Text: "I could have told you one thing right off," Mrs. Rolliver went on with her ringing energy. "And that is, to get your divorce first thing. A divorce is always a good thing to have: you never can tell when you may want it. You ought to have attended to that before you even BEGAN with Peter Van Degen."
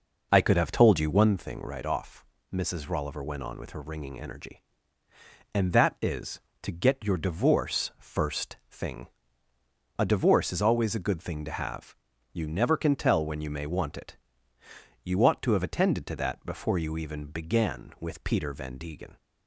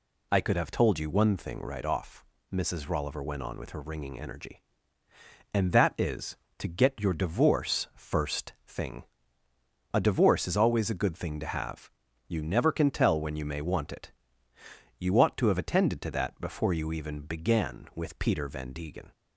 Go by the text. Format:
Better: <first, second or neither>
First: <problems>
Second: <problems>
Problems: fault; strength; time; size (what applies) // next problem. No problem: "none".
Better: second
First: starts louder than the rest; noticeable; until 1.4 s; 5 dB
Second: none